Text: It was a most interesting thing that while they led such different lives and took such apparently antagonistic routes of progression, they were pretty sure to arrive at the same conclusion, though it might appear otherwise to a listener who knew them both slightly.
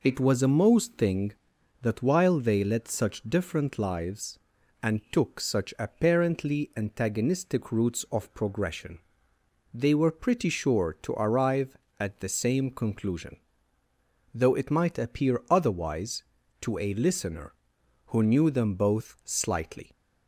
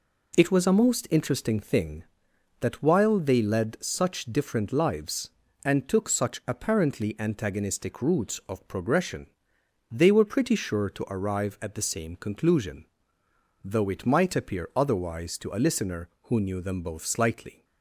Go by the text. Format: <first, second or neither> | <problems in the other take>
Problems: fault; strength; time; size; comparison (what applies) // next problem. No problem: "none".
second | skips "interesting"; at 0.9 s